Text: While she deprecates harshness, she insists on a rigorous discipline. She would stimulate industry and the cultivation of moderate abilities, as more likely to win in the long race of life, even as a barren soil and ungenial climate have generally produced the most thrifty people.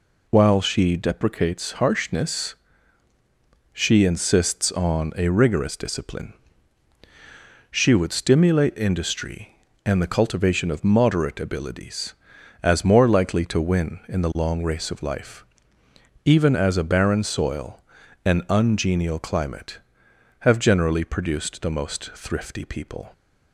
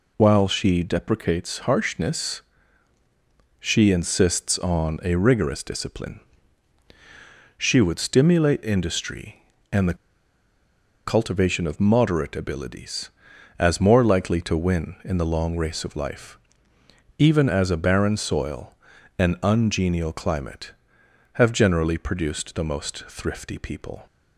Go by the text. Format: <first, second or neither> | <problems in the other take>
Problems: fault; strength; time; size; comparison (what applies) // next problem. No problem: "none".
first | pauses between "the" and "cultivation"; at 9.9 s; 1.1 s long